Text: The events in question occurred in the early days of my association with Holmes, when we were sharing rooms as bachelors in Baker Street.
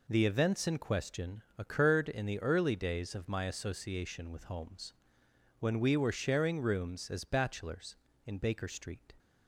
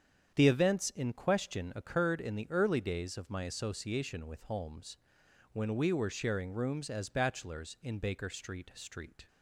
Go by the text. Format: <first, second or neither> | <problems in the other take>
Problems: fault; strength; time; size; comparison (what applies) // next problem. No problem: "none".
first | starts louder than the rest; strong; until 1.3 s; 8 dB // says "Street" twice; at 8.7 s